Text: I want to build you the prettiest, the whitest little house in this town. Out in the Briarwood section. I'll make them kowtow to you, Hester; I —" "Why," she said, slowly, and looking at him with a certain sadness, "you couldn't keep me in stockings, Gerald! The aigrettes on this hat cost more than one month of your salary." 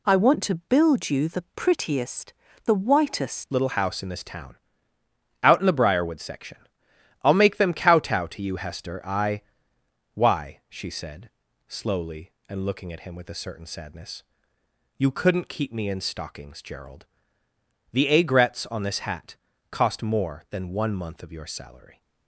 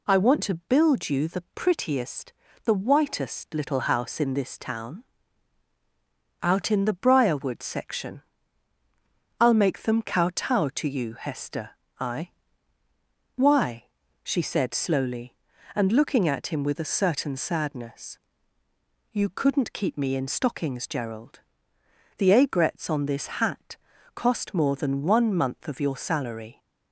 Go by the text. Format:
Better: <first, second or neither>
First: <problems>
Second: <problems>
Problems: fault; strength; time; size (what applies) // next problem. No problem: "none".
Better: second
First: changes voice at "little"; from 3.5 s on; 18.5 s long // pauses between "hat" and "cost"; slight; at 19.3 s; 0.34 s long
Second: pauses between "hat" and "cost"; at 23.7 s; 0.40 s long